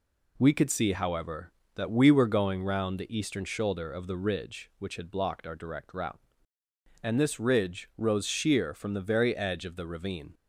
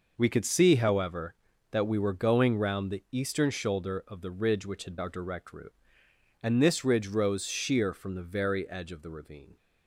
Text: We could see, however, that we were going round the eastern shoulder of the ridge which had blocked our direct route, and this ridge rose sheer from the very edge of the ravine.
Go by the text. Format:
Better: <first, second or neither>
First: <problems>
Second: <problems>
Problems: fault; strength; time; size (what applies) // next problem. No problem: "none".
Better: first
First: none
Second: skips "blocked"; at 4.9 s